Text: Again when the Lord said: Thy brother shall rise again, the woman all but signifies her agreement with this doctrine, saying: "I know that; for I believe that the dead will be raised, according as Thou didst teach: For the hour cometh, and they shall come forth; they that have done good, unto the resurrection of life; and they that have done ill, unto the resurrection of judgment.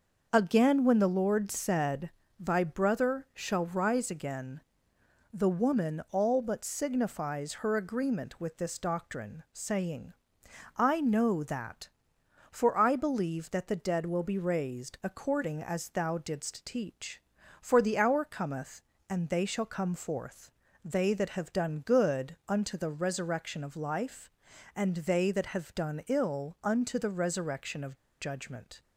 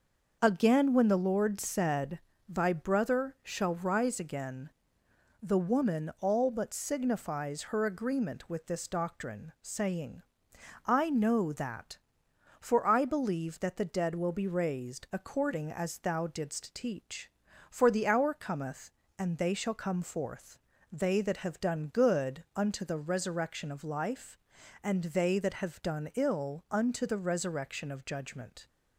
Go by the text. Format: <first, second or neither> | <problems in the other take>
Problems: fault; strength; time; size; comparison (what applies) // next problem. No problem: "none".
second | starts louder than the rest; until 1.3 s; 6 dB; also in the second // pauses between "of" and "judgment"; slight; at 27.9 s; 0.22 s long